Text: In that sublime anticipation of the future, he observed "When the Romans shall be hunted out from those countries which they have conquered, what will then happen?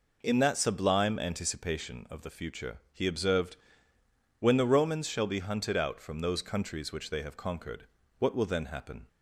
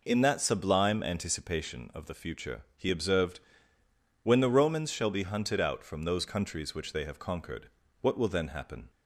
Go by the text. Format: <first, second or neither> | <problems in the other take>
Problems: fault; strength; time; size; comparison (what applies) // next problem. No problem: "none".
neither | pauses between "observed" and "When"; noticeable; the same in both